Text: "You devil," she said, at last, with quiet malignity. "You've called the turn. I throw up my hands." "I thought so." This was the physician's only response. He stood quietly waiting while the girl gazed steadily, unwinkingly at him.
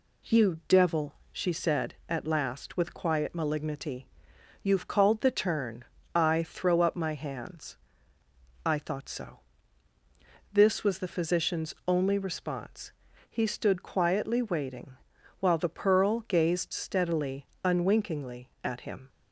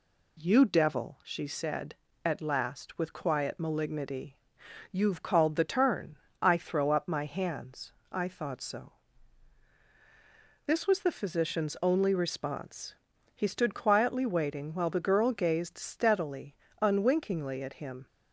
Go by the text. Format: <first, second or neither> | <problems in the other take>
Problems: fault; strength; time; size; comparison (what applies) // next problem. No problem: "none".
second | pauses between "waiting" and "while"; noticeable; at 14.9 s; 0.46 s long // says "pearl" for "girl"; at 15.6 s